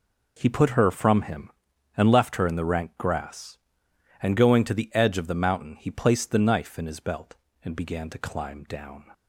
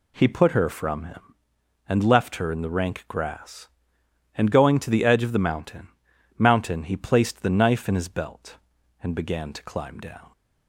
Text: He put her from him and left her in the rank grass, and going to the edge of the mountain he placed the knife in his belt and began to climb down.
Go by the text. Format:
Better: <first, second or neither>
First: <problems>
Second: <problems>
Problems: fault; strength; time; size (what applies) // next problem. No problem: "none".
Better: first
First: none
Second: says "mountain" twice; at 6.3 s